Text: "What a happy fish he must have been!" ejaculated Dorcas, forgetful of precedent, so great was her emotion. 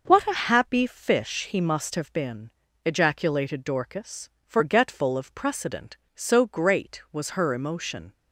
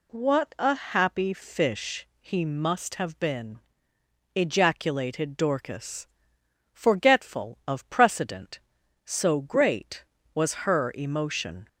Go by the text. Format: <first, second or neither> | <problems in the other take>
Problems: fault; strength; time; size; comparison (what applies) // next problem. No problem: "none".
neither | none